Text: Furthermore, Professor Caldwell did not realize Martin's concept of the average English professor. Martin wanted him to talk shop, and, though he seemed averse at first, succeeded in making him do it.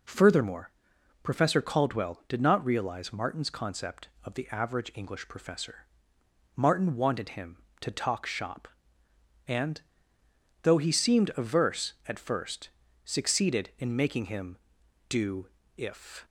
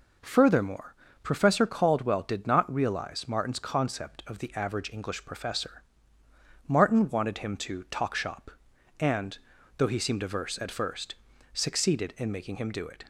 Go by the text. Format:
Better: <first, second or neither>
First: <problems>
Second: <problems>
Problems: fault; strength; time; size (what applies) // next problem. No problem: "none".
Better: second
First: says "if" for "it"; at 15.7 s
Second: none